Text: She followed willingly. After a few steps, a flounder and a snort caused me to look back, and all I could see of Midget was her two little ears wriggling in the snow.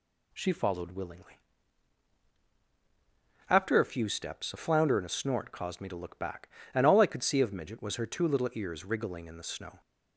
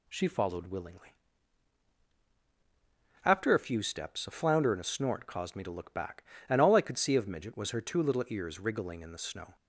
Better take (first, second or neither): neither